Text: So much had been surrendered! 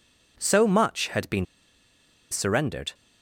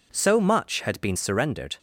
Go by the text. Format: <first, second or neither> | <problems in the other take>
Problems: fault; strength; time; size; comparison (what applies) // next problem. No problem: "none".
second | pauses between "been" and "surrendered"; noticeable; at 1.4 s; 0.87 s long